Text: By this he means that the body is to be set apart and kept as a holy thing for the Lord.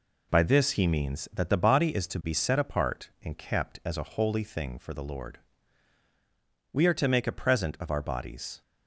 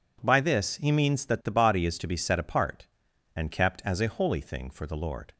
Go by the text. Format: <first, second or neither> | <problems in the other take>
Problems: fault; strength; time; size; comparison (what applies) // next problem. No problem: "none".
second | goes on to say "We are to make a present of our bodies"; strong; from 6.7 s on; 1.8 s long